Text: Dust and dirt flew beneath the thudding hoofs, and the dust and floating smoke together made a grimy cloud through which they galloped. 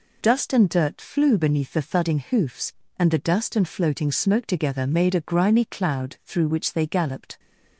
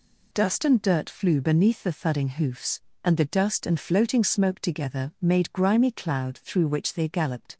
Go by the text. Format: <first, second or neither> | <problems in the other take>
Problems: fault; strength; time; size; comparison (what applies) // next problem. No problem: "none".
first | skips "a"; at 5.5 s